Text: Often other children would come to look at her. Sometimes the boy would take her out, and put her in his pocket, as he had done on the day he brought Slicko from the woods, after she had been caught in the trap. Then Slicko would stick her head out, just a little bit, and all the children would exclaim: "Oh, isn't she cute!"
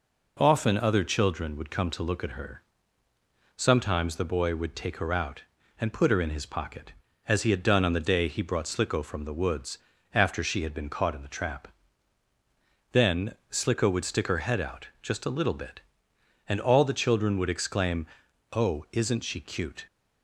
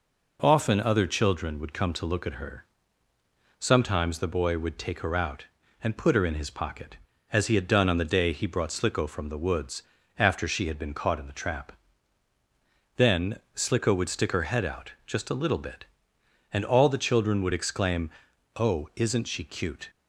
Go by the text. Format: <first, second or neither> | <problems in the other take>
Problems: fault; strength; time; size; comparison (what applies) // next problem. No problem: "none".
neither | pauses between "Then" and "Slicko"; slight; the same in both